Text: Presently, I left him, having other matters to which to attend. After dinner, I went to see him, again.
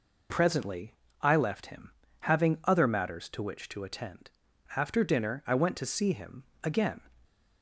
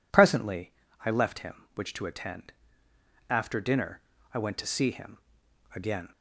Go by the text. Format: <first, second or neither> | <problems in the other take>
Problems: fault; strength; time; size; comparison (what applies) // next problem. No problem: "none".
first | skips "having other matters to"; at 1.7 s